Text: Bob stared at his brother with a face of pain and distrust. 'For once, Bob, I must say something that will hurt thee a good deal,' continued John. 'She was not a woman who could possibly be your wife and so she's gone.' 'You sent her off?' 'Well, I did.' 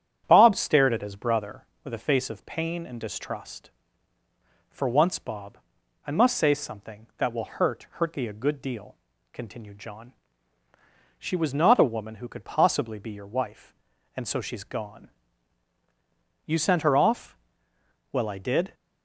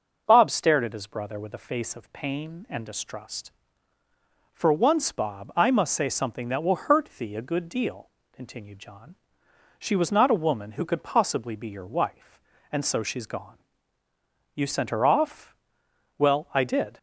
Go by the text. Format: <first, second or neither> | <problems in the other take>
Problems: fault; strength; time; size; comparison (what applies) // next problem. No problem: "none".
second | starts louder than the rest; strong; until 1.2 s; 9.5 dB // says "hurt" twice; at 7.9 s